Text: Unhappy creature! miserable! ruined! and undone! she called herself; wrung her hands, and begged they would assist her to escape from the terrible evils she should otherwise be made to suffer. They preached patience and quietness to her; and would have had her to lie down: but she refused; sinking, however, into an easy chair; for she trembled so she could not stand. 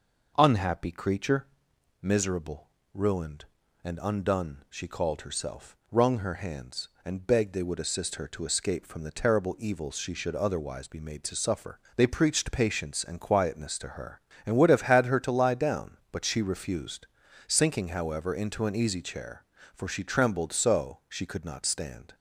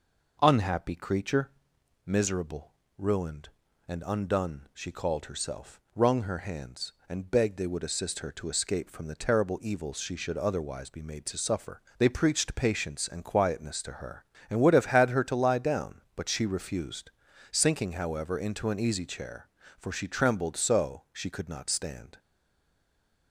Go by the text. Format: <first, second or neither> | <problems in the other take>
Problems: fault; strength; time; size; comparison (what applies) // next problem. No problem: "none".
first | stays silent after the last word; from 22.1 s on; 1.2 s long